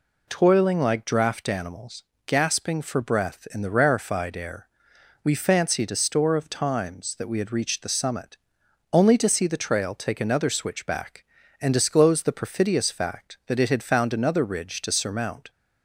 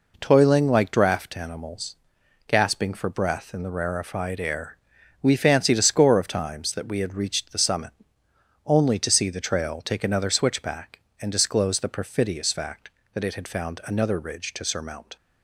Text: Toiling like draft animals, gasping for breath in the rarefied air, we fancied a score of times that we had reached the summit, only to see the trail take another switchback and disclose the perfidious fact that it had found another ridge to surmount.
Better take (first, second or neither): second